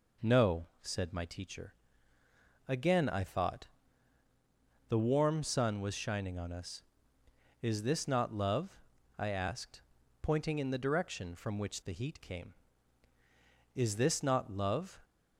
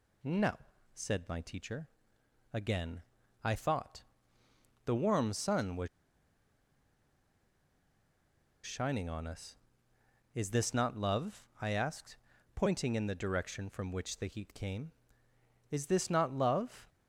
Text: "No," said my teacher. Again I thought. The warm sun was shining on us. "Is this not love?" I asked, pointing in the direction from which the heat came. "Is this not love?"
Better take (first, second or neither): first